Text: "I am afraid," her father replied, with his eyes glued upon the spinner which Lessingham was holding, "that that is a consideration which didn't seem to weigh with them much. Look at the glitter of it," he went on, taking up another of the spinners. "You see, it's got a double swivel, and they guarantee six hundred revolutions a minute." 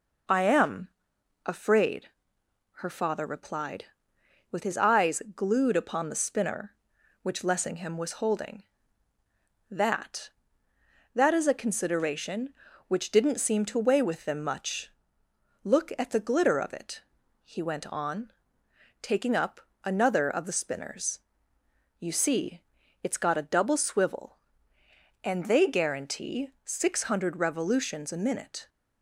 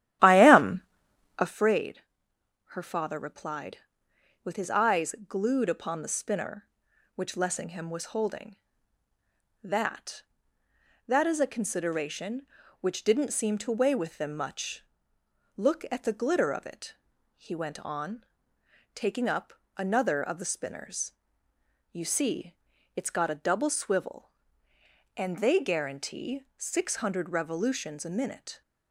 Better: first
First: pauses between "am" and "afraid"; noticeable; at 0.8 s; 0.56 s long // pauses between "up" and "another"; slight; at 19.6 s; 0.24 s long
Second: starts louder than the rest; strong; until 1.7 s; 13 dB // pauses between "am" and "afraid"; noticeable; at 0.8 s; 0.56 s long // pauses between "up" and "another"; slight; at 19.5 s; 0.24 s long

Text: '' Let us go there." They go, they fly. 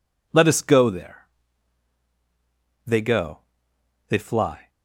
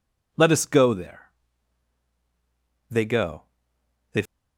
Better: first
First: none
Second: stops before "fly"; at 4.2 s

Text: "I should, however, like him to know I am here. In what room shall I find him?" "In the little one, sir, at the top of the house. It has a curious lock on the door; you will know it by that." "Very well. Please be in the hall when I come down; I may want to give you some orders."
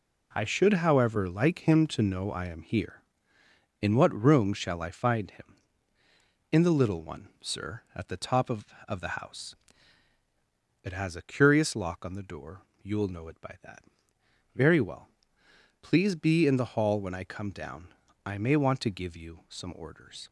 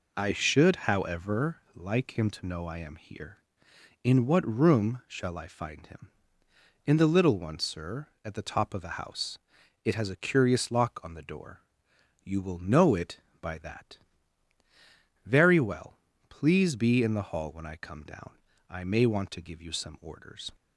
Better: second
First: says "of" twice; at 8.8 s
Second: none

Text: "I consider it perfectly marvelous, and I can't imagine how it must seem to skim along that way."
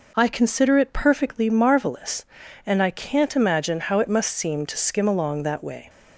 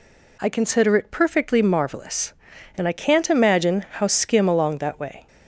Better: first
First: none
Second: skips "it must seem to"; at 4.0 s

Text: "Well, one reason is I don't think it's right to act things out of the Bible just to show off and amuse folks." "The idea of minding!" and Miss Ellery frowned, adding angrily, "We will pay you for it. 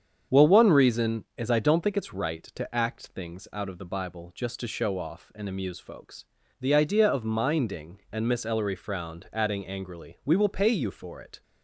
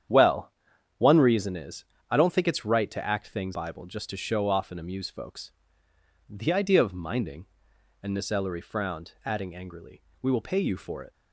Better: first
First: starts louder than the rest; strong; until 1.4 s; 7.5 dB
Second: starts louder than the rest; strong; until 1.5 s; 9 dB // pauses between "is" and "I"; slight; at 1.8 s; 0.24 s long // skips "out of the"; at 3.5 s

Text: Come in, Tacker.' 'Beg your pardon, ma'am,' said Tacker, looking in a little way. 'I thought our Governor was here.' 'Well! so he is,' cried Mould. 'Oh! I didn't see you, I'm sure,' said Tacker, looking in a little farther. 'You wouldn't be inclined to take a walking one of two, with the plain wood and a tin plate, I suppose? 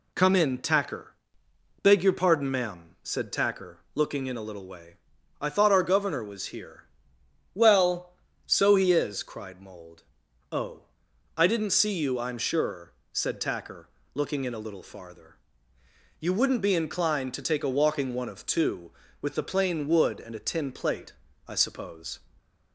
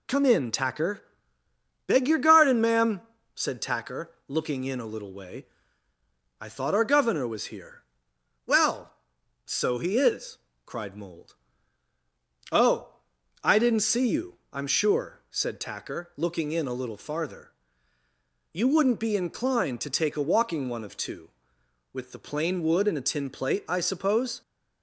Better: first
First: none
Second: says "garden" for "pardon"; at 2.1 s

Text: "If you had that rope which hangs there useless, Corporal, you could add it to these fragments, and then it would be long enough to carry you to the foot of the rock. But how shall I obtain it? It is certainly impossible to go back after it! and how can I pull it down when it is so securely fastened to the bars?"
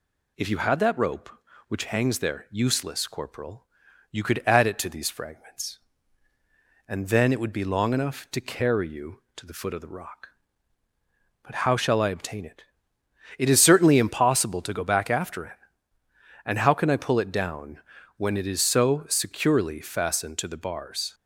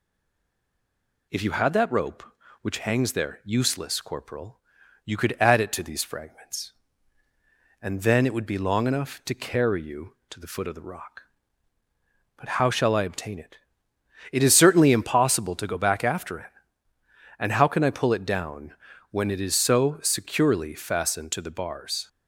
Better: first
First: pauses between "down" and "when"; at 17.7 s; 0.38 s long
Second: stays silent before the first word; noticeable; until 1.2 s; 1.2 s long // pauses between "down" and "when"; at 18.7 s; 0.38 s long

